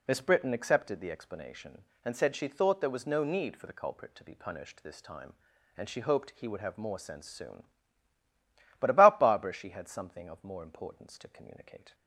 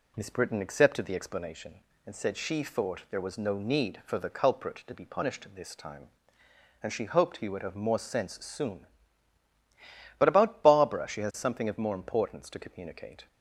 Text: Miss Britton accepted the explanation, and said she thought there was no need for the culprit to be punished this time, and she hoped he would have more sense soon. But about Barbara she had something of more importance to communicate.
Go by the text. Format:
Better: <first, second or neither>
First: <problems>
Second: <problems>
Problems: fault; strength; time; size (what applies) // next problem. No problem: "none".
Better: first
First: none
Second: says "has" for "had"; at 11.2 s